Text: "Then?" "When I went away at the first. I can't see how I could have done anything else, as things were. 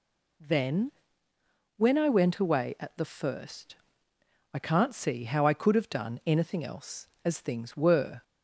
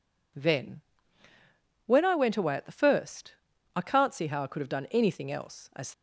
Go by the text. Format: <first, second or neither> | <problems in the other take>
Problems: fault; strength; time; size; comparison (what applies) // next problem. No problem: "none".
first | stops before "things were"; at 5.9 s